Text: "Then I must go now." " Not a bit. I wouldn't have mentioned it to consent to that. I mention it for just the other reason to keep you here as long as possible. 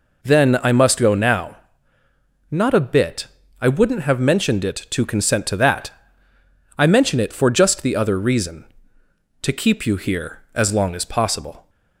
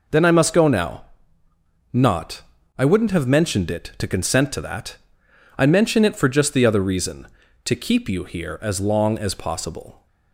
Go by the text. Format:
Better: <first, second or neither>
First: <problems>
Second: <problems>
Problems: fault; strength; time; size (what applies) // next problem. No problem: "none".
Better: first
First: none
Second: skips "a bit"; at 2.5 s